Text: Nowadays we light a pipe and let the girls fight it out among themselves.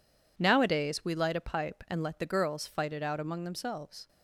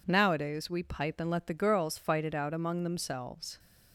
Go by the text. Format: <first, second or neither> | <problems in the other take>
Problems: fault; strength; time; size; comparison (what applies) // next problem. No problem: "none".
first | skips "light a"; at 0.8 s